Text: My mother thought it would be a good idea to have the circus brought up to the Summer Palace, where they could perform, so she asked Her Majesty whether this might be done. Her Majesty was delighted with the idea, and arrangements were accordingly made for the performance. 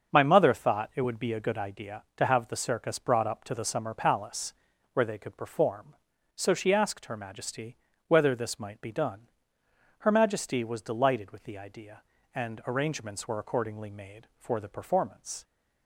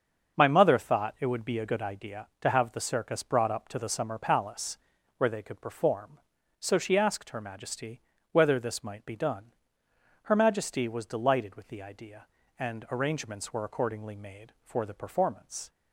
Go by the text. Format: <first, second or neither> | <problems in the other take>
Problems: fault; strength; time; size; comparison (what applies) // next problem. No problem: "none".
neither | starts louder than the rest; the same in both // pauses between "Majesty" and "whether"; slight; the same in both